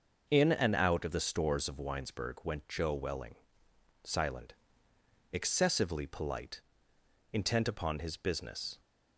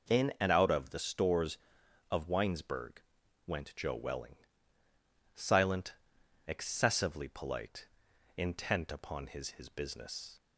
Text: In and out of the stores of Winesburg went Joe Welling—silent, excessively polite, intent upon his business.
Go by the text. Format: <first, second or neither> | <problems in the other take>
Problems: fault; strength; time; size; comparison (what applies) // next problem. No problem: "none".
first | pauses between "Winesburg" and "went"; at 3.0 s; 0.44 s long // says "his" twice; at 9.5 s